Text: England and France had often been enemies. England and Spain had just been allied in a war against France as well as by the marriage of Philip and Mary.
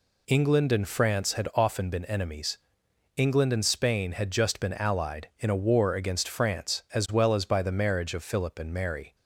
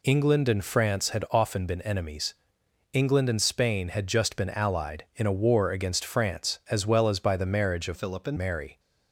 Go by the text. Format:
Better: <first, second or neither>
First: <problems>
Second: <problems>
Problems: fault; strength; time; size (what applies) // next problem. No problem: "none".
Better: first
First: none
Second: changes voice from "Philip" to "and"; from 7.9 to 8.3 s; 0.4 s long